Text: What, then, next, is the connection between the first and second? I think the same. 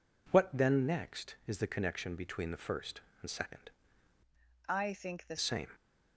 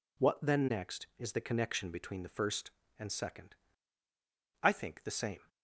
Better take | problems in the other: second | changes voice from "I" to "the"; from 4.6 to 5.3 s; 0.7 s long

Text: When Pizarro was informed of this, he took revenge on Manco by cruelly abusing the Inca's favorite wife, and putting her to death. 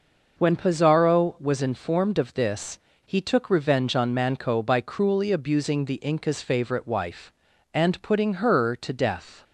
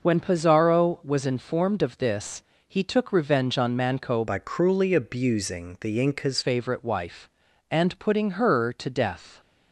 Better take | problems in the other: first | changes voice from "by" to "Inca's"; from 4.2 to 6.3 s; 2.1 s long

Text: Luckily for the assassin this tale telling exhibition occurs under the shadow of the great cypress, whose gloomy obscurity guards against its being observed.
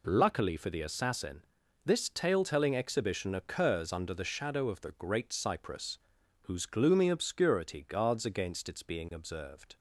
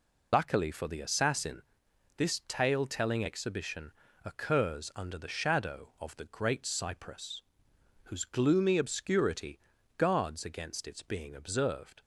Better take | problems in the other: first | loses the start of "Luckily"; at 0.3 s; 95 ms // pauses between "assassin" and "this"; noticeable; at 1.6 s; 0.56 s long; also in the first // pauses between "exhibition" and "occurs"; slight; at 3.9 s; 0.34 s long // pauses between "obscurity" and "guards"; at 9.5 s; 0.38 s long

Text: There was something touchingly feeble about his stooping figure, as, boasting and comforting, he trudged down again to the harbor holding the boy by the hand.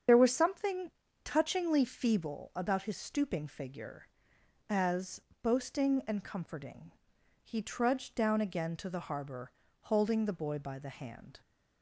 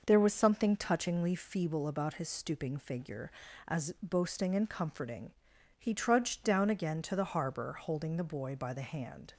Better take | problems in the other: second | loses the start of "There"; at 0.0 s; 45 ms // starts louder than the rest; strong; until 1.4 s; 7.5 dB // pauses between "something" and "touchingly"; slight; at 0.9 s; 0.34 s long // pauses between "harbor" and "holding"; slight; at 9.5 s; 0.32 s long

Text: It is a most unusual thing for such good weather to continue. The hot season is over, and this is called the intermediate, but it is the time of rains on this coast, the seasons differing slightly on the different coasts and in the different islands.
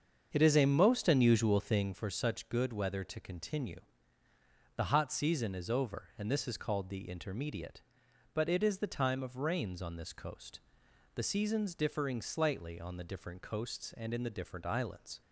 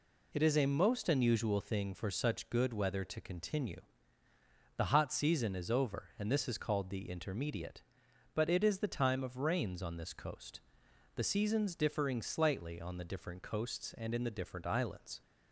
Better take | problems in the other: second | starts louder than the rest; until 2.0 s; 7 dB

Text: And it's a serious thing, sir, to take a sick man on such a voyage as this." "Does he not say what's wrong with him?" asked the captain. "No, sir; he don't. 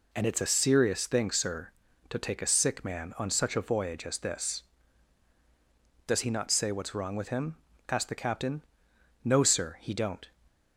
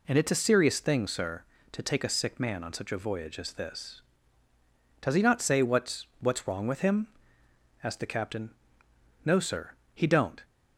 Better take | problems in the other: first | says "what's" twice; at 6.1 s

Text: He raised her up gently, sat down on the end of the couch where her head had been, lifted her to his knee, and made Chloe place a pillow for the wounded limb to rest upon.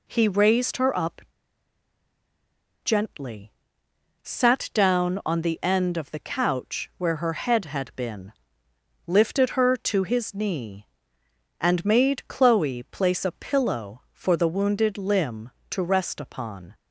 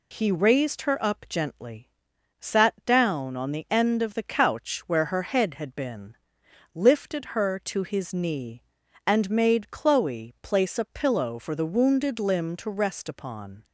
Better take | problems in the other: second | pauses between "up" and "gently"; strong; at 1.1 s; 1.6 s long

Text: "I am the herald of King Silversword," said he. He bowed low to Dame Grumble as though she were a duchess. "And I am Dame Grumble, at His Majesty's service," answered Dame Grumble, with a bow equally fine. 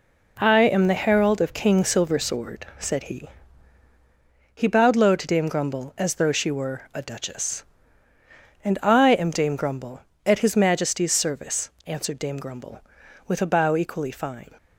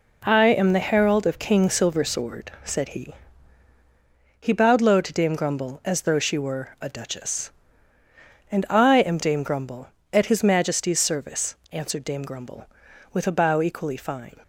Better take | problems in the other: neither | none

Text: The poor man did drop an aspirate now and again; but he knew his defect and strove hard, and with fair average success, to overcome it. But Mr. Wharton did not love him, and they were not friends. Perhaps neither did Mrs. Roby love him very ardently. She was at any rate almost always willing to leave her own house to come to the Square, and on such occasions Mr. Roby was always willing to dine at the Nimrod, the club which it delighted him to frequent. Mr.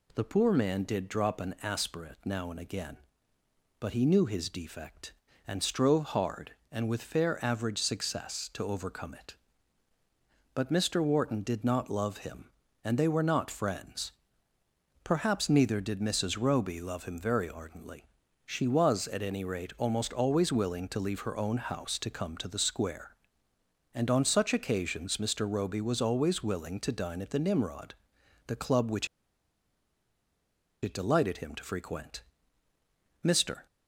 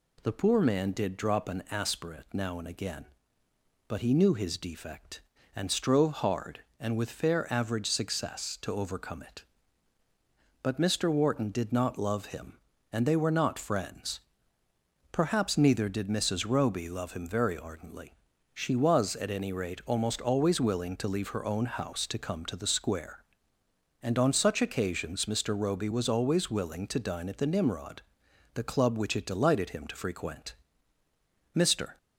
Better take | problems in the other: second | pauses between "which" and "it"; strong; at 29.0 s; 1.7 s long

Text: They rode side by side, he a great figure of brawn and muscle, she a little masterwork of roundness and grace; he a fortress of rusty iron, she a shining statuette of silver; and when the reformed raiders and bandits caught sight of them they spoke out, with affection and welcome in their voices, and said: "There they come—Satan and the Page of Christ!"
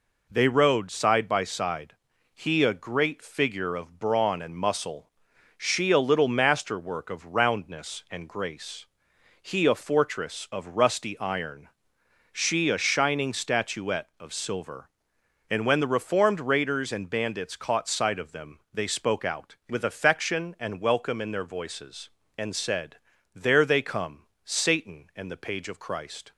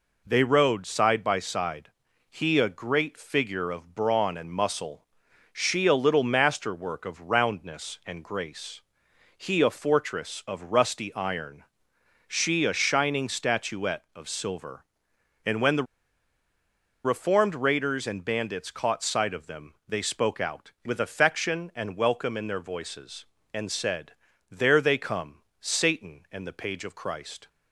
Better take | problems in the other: first | pauses between "the" and "reformed"; at 15.8 s; 1.2 s long

